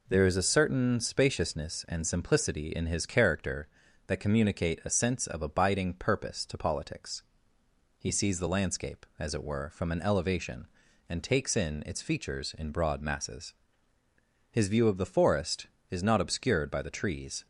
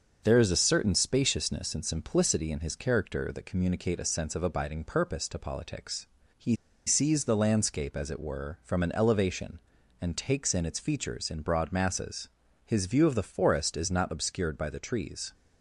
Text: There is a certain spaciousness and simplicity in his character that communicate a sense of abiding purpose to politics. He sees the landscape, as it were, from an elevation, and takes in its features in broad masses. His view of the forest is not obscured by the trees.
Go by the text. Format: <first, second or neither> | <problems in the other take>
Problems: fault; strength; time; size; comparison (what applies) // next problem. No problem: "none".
first | starts louder than the rest; until 1.2 s; 6.5 dB // pauses between "He" and "sees"; slight; at 6.5 s; 0.32 s long